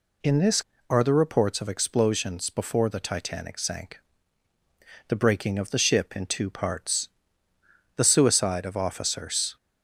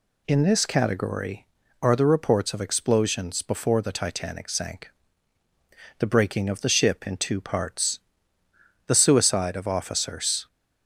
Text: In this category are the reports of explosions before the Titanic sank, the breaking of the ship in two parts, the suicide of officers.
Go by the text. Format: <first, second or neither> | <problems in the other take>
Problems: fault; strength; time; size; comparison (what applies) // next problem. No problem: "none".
second | skips "category"; at 0.7 s